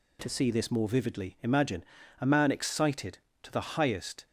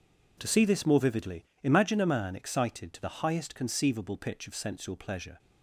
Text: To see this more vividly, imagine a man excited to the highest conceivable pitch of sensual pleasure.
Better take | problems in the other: second | pauses between "imagine" and "a"; at 1.8 s; 0.38 s long // stops before "conceivable pitch of sensual pleasure"; at 4.2 s

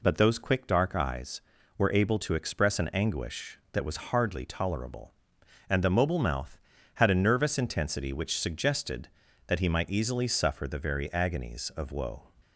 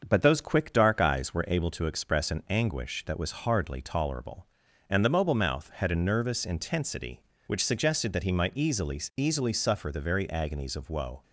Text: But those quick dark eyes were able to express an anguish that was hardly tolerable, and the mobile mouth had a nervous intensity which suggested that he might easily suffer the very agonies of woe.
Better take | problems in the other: first | starts louder than the rest; until 1.0 s; 7 dB // says "easily" twice; at 9.1 s

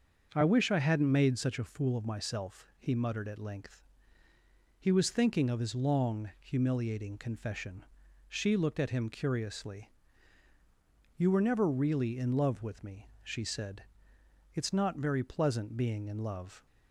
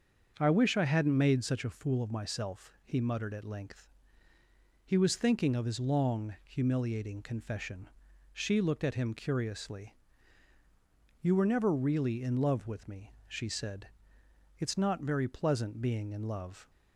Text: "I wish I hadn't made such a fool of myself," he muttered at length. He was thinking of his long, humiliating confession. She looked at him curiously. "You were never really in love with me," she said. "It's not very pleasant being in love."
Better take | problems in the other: neither | starts louder than the rest; the same in both

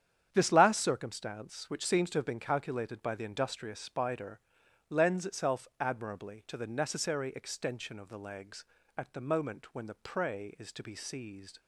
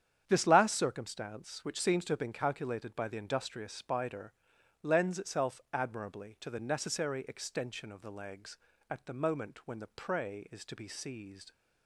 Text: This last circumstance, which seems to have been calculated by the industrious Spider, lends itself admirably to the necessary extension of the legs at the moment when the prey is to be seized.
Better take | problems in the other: neither | starts louder than the rest; strong; the same in both

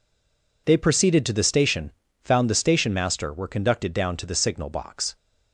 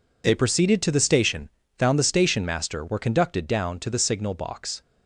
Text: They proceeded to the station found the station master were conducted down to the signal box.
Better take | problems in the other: second | stays silent before the first word; slight; until 0.6 s; 0.6 s long // pauses between "station" and "found"; slight; at 1.9 s; 0.32 s long; slight in the second

